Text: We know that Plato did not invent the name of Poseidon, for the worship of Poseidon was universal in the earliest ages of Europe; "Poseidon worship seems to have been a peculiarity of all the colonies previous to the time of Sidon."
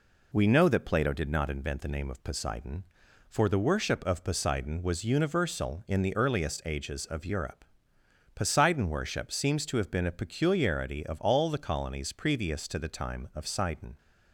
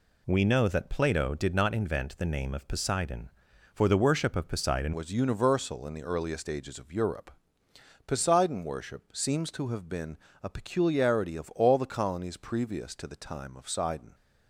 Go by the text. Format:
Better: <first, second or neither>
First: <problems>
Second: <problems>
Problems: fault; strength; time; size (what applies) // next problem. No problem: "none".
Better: first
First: none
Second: changes voice at "was"; from 4.9 s on; 9.2 s long // pauses between "been" and "a"; slight; at 10.1 s; 0.24 s long